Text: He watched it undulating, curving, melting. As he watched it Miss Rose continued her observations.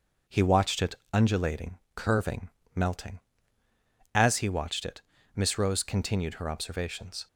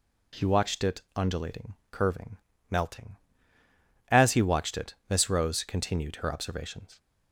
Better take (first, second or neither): second